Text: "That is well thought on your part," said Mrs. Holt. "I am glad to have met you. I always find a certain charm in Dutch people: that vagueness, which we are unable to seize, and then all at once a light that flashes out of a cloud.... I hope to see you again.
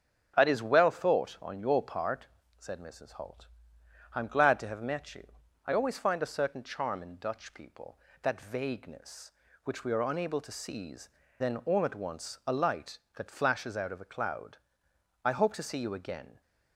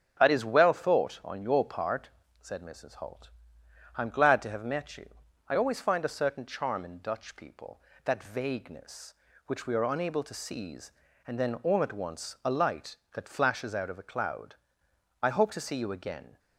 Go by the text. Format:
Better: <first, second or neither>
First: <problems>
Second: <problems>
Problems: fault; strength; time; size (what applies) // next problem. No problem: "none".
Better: second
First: starts louder than the rest; strong; until 1.3 s; 7.5 dB // skips "and"; at 11.2 s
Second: starts louder than the rest; strong; until 1.2 s; 7.5 dB